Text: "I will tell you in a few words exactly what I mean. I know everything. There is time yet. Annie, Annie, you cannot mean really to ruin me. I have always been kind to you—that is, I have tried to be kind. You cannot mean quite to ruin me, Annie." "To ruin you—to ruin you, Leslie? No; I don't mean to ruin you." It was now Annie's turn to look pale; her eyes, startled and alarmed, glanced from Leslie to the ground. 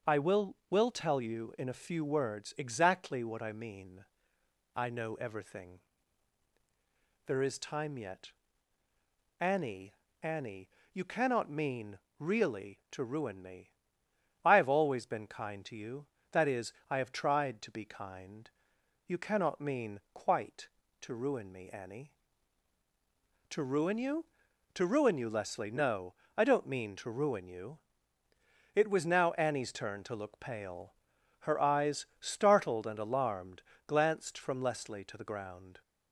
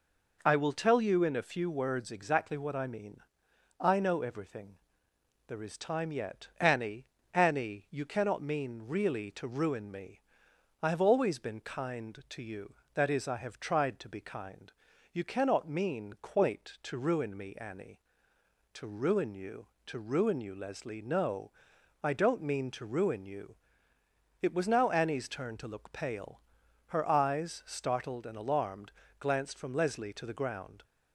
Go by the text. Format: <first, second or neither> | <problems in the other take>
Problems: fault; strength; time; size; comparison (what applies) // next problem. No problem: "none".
second | starts louder than the rest; until 1.2 s; 6.5 dB // says "will" twice; at 0.6 s // pauses between "mean" and "really"; slight; at 11.9 s; 0.18 s long